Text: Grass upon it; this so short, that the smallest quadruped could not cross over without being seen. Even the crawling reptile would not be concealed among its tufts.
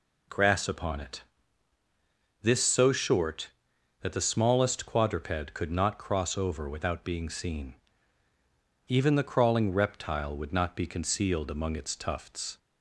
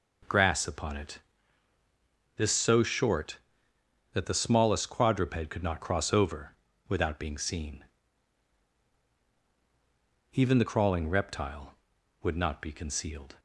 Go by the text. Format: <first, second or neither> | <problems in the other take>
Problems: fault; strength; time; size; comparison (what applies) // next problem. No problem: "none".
first | pauses between "over" and "without"; slight; at 6.5 s; 0.34 s long // stops before "among its tufts"; at 13.3 s